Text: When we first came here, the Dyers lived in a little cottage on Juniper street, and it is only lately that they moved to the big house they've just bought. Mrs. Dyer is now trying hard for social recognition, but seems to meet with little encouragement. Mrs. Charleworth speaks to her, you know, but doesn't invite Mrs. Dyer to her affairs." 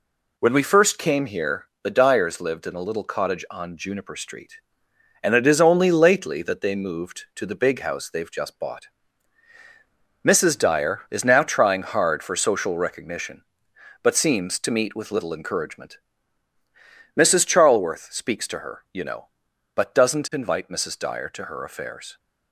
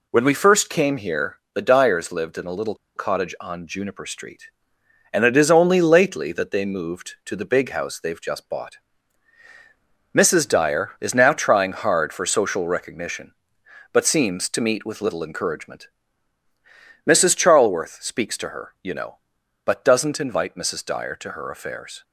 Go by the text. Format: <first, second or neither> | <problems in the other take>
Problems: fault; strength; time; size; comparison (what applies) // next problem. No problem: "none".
first | pauses between "little" and "cottage"; slight; at 2.7 s; 0.21 s long